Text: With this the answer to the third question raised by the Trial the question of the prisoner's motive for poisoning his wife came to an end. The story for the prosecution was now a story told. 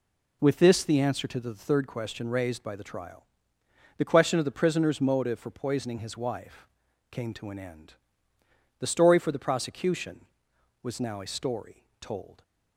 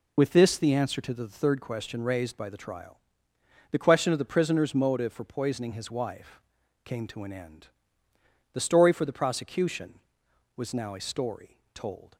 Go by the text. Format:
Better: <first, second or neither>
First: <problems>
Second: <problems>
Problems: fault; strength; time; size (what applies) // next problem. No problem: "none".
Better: first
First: pauses between "Trial" and "the"; noticeable; at 3.2 s; 0.72 s long // pauses between "wife" and "came"; at 6.6 s; 0.44 s long // pauses between "story" and "told"; slight; at 11.8 s; 0.18 s long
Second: loses the start of "With"; at 0.1 s; 40 ms // pauses between "Trial" and "the"; noticeable; at 2.9 s; 0.72 s long // pauses between "wife" and "came"; at 6.3 s; 0.44 s long // pauses between "story" and "told"; slight; at 11.5 s; 0.18 s long